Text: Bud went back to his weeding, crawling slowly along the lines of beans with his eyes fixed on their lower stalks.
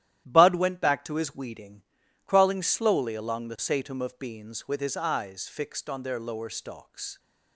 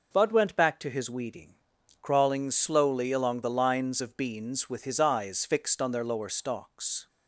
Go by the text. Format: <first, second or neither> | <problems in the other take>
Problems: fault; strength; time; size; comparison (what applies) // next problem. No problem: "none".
second | starts louder than the rest; strong; until 1.3 s; 12.5 dB // says "satum" for "lines"; at 3.5 s